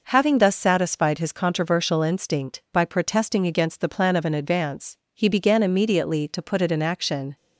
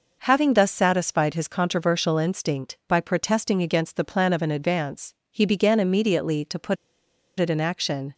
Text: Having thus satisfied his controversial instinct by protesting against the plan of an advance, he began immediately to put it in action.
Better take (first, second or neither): first